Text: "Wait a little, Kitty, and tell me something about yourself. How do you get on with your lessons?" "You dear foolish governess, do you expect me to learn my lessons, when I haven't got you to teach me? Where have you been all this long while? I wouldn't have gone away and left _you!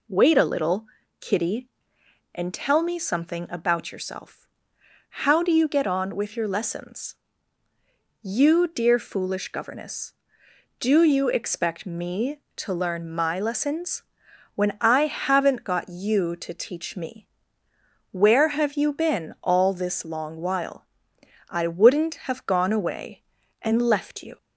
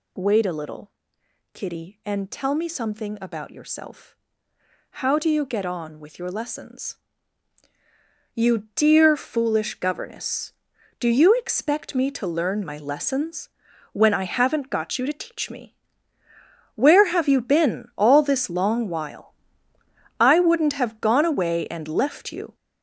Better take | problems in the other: first | gets louder; throughout; 7 dB

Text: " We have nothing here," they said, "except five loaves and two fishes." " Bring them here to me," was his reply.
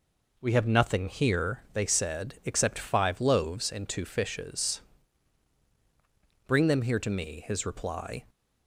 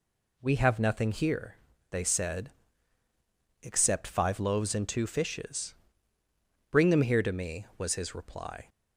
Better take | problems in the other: second | skips "was"; at 7.4 s

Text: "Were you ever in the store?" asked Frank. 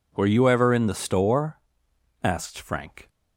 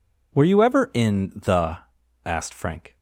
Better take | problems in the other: first | skips "store"; at 2.0 s

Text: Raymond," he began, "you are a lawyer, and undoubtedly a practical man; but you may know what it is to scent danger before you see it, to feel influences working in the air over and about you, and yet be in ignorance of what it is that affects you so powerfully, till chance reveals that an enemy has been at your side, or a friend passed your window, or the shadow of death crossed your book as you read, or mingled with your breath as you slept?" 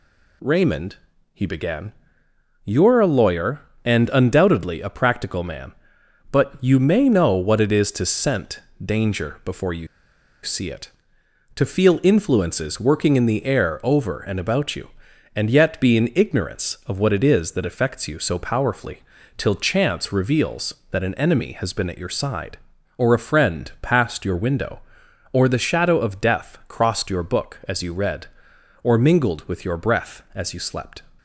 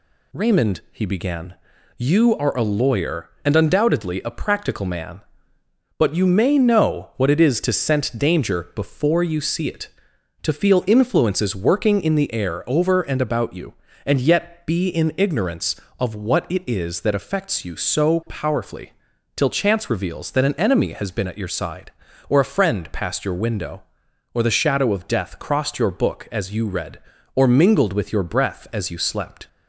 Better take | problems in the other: second | pauses between "scent" and "danger"; slight; at 8.5 s; 0.24 s long // pauses between "you" and "see"; noticeable; at 9.8 s; 0.56 s long

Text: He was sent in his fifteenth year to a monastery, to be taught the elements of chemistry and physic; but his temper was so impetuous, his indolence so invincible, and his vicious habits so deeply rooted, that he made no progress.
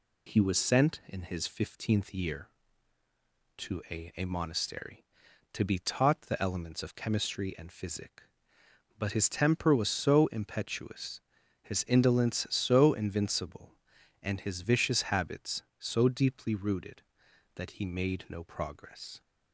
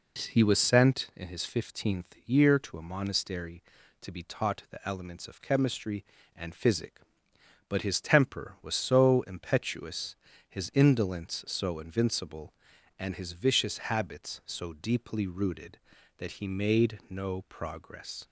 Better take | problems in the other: second | says "a" twice; at 4.1 s

